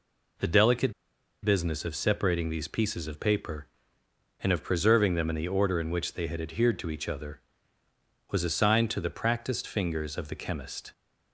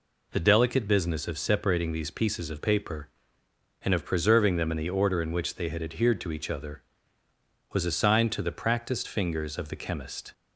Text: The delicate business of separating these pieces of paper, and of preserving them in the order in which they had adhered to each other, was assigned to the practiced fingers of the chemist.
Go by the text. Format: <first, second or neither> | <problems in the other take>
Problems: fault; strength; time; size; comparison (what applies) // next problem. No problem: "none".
second | pauses between "delicate" and "business"; noticeable; at 0.9 s; 0.50 s long